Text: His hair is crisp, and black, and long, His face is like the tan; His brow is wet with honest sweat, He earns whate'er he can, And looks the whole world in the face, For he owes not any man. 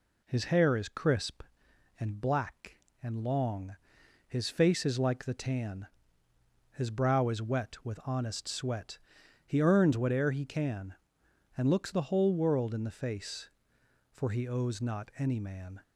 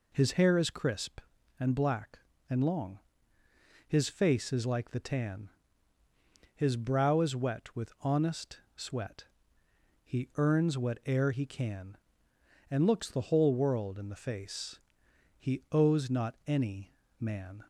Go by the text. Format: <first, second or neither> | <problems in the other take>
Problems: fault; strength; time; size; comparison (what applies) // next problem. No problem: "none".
first | pauses between "honest" and "sweat"; slight; at 8.5 s; 0.16 s long // skips "For"; at 15.0 s // pauses between "any" and "man"; slight; at 16.9 s; 0.20 s long